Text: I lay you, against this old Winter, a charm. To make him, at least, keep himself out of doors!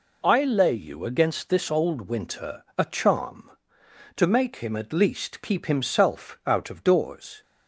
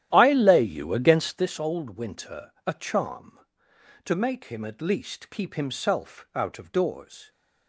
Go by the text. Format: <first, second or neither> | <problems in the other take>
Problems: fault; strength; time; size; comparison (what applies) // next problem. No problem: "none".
first | starts louder than the rest; strong; until 1.5 s; 12 dB